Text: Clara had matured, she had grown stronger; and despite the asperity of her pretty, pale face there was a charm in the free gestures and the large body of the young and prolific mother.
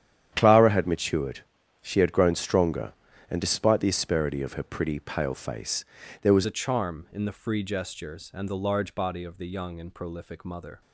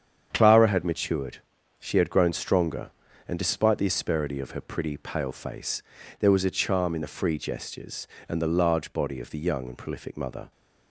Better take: second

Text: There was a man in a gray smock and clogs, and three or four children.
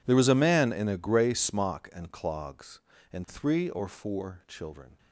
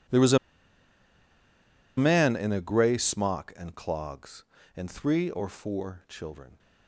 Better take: first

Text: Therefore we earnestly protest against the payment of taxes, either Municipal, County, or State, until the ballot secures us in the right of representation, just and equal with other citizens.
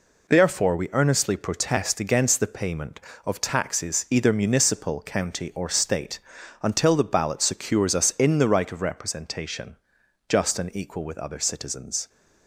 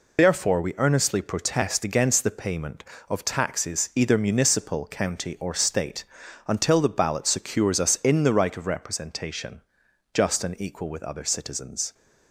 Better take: first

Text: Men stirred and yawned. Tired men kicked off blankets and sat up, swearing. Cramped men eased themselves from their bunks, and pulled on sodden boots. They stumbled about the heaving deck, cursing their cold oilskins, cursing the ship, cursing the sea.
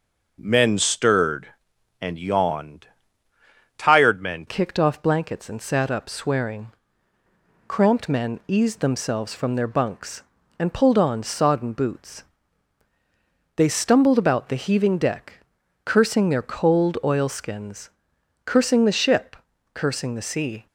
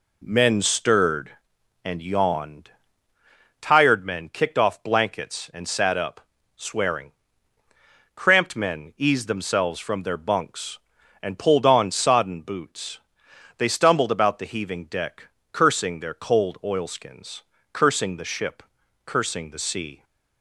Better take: second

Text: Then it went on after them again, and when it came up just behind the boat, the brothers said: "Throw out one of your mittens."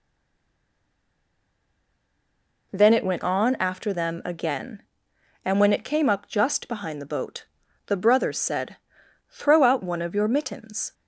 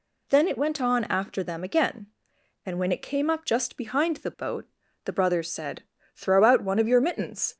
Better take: second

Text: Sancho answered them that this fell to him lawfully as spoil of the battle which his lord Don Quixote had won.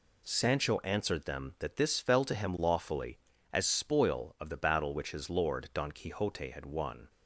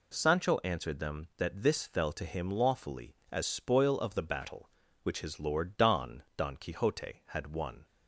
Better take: first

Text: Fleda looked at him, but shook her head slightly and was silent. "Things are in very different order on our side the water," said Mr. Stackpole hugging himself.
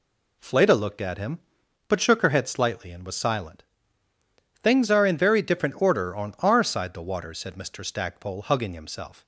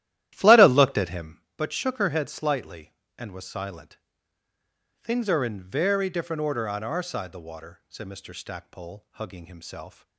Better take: first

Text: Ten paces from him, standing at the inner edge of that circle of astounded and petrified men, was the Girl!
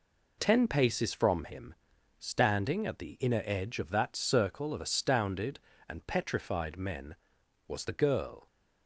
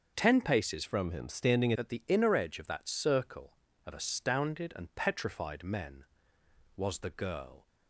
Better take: first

